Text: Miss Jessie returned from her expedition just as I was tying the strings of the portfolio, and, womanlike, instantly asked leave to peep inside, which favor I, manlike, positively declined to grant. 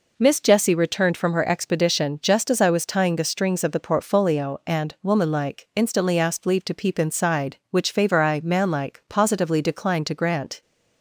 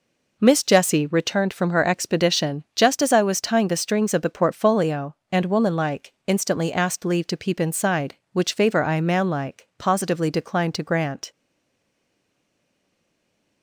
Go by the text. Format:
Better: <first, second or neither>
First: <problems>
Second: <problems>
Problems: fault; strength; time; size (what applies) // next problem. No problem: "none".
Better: first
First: none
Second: stays silent after the last word; from 11.3 s on; 2.3 s long